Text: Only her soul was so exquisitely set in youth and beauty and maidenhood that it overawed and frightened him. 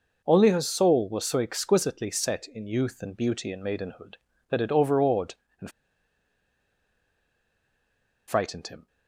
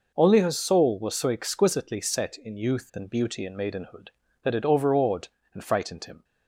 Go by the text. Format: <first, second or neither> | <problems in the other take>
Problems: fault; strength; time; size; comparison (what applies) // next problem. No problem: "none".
second | pauses between "and" and "frightened"; strong; at 5.6 s; 2.5 s long